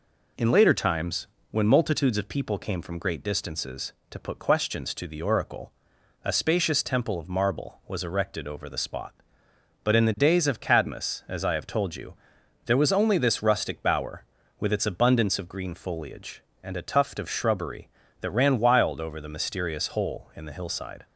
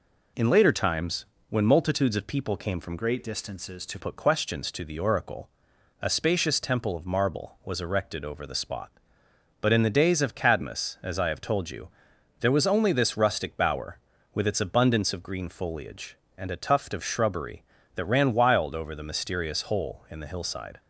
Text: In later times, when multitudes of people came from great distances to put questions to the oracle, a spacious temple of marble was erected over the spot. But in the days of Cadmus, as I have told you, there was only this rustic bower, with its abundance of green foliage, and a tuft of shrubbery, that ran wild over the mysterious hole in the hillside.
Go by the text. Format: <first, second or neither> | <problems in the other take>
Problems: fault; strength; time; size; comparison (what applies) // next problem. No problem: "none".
first | changes voice from "great" to "to"; from 2.9 to 3.9 s; 1.0 s long